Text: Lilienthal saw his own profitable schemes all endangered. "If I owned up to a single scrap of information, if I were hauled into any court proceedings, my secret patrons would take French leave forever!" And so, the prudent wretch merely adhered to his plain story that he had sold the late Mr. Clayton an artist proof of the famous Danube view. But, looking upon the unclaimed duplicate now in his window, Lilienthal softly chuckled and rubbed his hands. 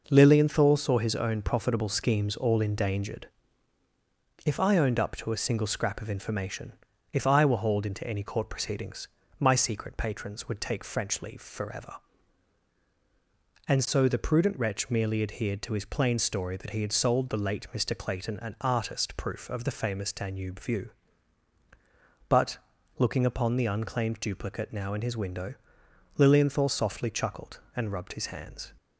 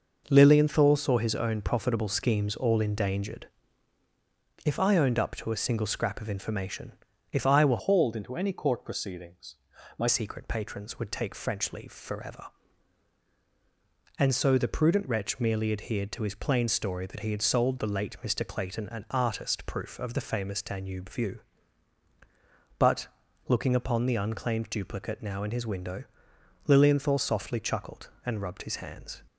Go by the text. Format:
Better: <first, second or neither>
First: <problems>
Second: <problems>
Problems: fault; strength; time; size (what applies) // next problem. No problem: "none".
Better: first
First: none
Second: changes voice from "hauled" to "my"; from 7.7 to 10.0 s; 2.3 s long